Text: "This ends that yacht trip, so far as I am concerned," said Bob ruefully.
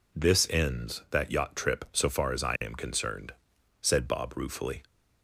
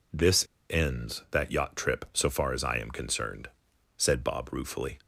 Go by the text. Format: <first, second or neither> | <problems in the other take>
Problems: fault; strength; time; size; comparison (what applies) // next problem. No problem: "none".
first | pauses between "This" and "ends"; slight; at 0.4 s; 0.25 s long